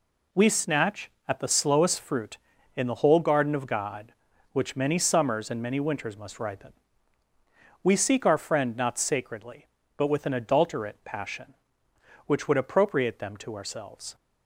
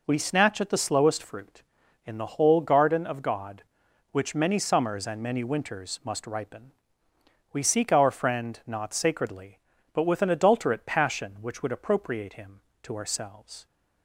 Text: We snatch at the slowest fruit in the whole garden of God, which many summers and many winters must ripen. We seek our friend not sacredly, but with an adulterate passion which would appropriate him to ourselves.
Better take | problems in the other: second | says "them" for "him"; at 13.1 s

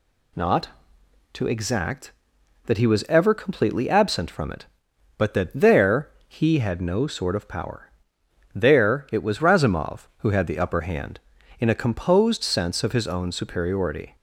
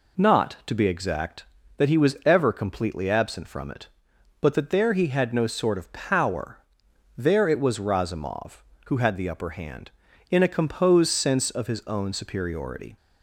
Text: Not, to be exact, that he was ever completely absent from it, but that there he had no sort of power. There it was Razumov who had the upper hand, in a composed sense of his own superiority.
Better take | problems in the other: second | skips "be"; at 1.4 s // pauses between "there" and "he"; slight; at 6.0 s; 0.18 s long

